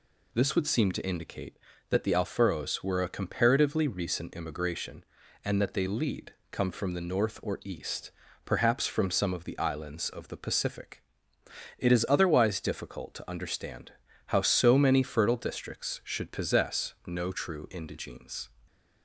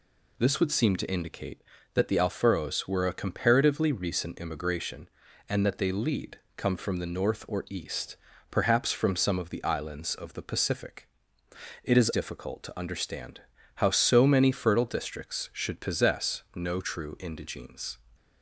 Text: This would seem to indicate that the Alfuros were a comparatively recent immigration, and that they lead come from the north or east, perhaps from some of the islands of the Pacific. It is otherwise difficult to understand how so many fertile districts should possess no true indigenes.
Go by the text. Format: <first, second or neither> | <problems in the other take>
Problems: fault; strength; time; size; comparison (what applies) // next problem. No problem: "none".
first | pauses between "lead" and "come"; slight; at 6.3 s; 0.18 s long; slight in the first // skips "otherwise"; at 12.1 s // pauses between "understand" and "how"; slight; at 13.4 s; 0.34 s long; slight in the first